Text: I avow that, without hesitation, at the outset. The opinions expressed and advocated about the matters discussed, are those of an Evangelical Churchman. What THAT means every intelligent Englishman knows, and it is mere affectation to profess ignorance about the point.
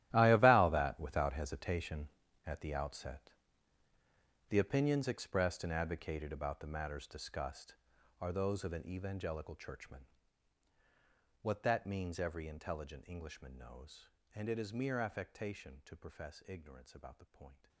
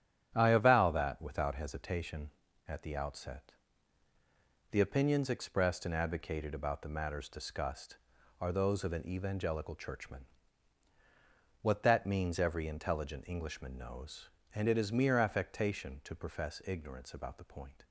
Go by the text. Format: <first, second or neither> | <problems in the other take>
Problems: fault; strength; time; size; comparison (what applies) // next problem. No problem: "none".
second | gets quieter; strong; throughout; 16 dB // starts louder than the rest; strong; until 1.1 s; 13.5 dB; strong in the second